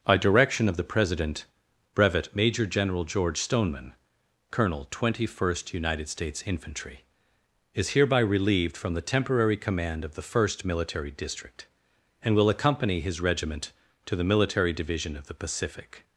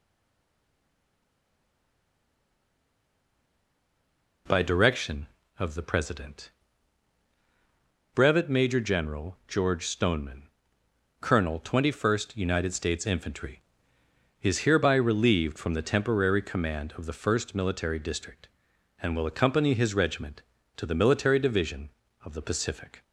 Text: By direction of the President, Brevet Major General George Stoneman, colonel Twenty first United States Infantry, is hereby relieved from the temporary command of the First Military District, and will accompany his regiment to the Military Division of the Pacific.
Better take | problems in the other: first | stays silent before the first word; strong; until 4.4 s; 4.4 s long

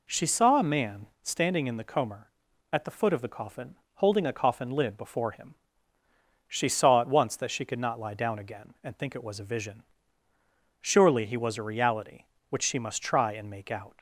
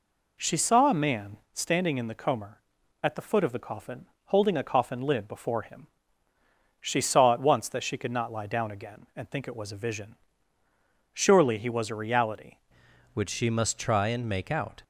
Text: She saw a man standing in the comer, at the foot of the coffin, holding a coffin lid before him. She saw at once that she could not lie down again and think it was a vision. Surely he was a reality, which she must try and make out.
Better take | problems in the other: first | pauses between "man" and "standing"; slight; at 1.3 s; 0.18 s long; slight in the first // changes voice at "which"; from 13.1 s on; 1.7 s long

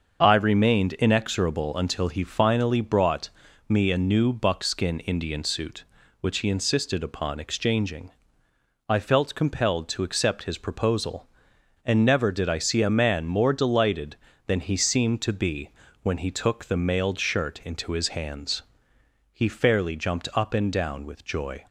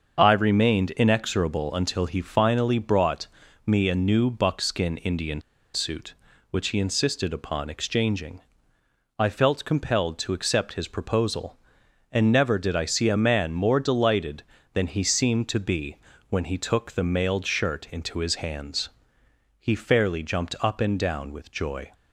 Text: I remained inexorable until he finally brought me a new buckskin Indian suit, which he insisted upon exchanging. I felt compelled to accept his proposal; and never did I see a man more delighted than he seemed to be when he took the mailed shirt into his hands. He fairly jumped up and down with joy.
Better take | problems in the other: first | starts louder than the rest; until 1.1 s; 6.5 dB; also in the first // pauses between "brought" and "me"; at 3.2 s; 0.38 s long; also in the first // pauses between "Indian" and "suit"; slight; at 5.4 s; 0.33 s long // pauses between "be" and "when"; slight; at 15.9 s; 0.32 s long; slight in the first

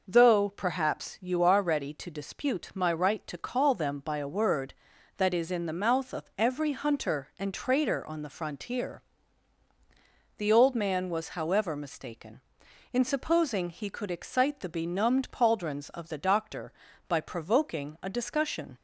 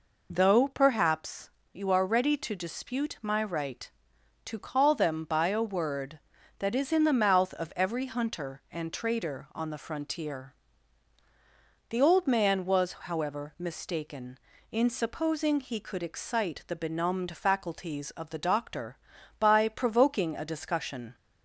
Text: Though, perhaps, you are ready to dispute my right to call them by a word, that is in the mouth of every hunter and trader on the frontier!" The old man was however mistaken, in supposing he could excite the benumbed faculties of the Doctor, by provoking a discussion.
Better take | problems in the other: second | says "pauldrons" for "faculties"; at 15.3 s

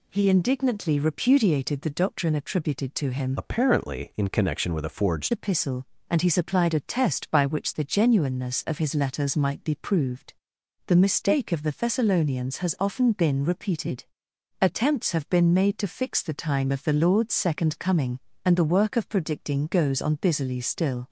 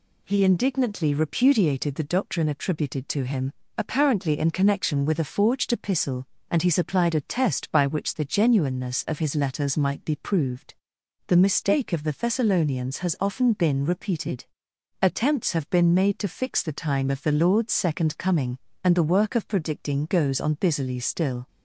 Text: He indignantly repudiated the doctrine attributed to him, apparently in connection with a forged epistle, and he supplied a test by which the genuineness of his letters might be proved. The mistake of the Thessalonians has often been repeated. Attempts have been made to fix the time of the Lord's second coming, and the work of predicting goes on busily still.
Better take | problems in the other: second | changes voice from "apparently" to "forged"; from 3.3 to 5.3 s; 2.0 s long

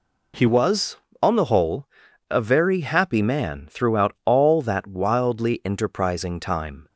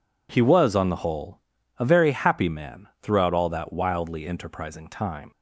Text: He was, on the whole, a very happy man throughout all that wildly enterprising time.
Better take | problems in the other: second | changes voice at "was"; from 0.4 s on; 6.4 s long

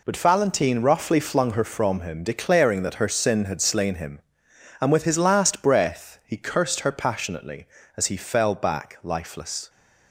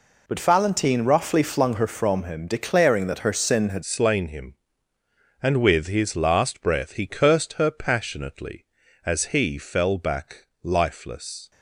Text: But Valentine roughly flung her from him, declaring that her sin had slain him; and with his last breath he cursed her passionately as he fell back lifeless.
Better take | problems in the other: first | changes voice at "slain"; from 3.8 s on; 7.7 s long // pauses between "back" and "lifeless"; slight; at 10.4 s; 0.16 s long

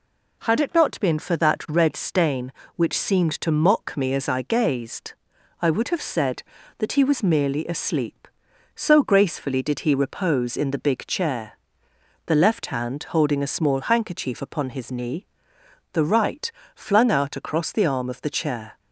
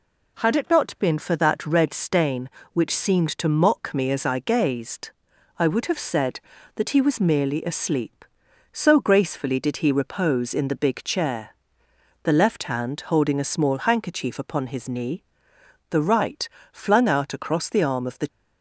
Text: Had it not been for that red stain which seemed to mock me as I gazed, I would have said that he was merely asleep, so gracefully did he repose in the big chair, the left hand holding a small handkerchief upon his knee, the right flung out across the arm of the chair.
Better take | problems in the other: first | pauses between "right" and "flung"; slight; at 16.4 s; 0.24 s long; slight in the first // stops before "chair"; at 18.2 s

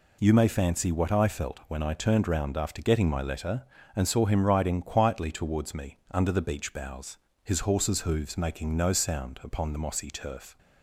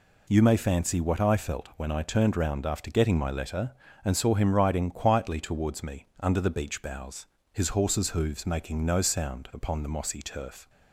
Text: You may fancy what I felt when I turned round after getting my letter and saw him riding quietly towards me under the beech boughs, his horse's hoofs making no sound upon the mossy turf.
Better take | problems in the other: neither | pauses between "me" and "under"; slight; the same in both

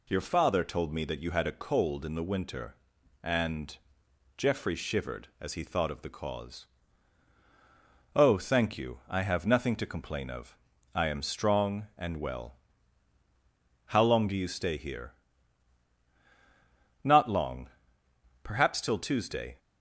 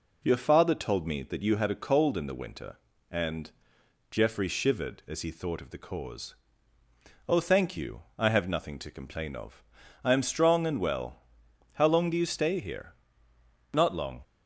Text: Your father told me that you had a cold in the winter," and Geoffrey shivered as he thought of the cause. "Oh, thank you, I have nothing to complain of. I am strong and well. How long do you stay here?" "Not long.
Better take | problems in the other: second | pauses between "and" and "Geoffrey"; noticeable; at 3.7 s; 0.62 s long; noticeable in the second // goes on to say "Perhaps till Tuesday"; noticeable; from 18.4 s on; 1.1 s long

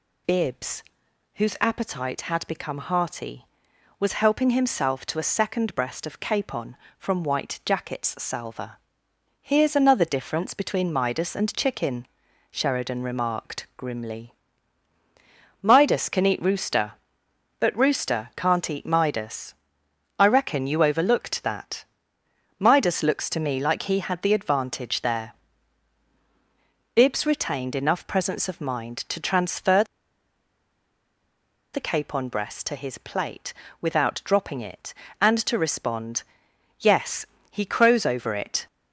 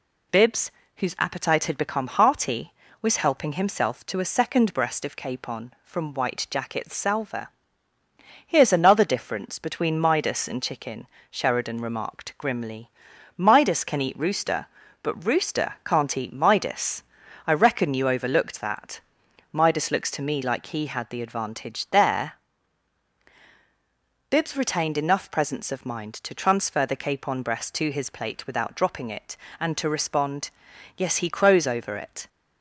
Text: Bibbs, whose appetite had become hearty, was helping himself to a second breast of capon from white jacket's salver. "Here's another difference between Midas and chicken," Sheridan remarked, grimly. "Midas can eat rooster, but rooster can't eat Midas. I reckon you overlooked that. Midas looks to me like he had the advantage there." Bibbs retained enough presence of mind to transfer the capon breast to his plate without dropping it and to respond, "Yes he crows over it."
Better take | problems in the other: second | pauses between "transfer" and "the"; strong; at 29.8 s; 1.8 s long // pauses between "plate" and "without"; slight; at 33.5 s; 0.28 s long // pauses between "Yes" and "he"; slight; at 37.2 s; 0.24 s long

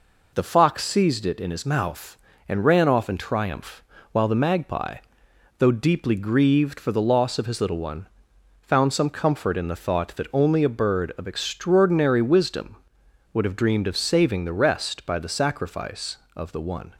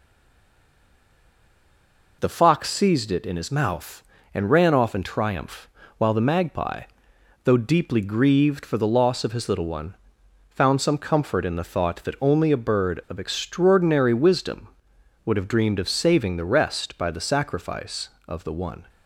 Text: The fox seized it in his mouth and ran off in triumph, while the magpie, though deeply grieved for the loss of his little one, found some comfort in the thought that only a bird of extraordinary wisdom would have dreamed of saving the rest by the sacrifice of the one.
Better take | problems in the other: first | stays silent before the first word; until 2.1 s; 2.1 s long

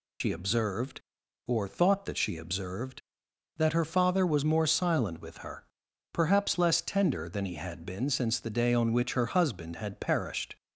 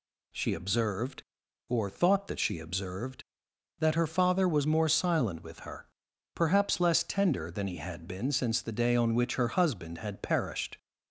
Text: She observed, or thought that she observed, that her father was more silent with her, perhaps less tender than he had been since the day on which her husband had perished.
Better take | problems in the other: second | loses the start of "She"; at 0.2 s; 85 ms

